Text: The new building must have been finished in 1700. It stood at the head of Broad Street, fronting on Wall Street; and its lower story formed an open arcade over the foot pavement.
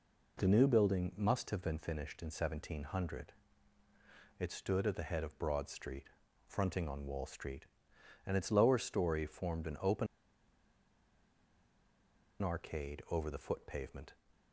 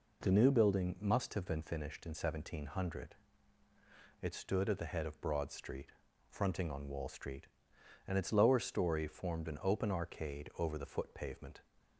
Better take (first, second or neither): second